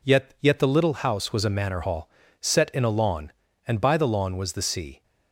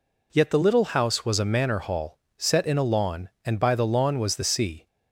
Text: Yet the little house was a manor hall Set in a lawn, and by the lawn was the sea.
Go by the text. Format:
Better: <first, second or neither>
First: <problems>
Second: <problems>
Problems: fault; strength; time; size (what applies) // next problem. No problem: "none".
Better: second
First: says "Yet" twice; at 0.4 s // pauses between "hall" and "Set"; slight; at 2.0 s; 0.36 s long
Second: pauses between "hall" and "Set"; slight; at 2.1 s; 0.24 s long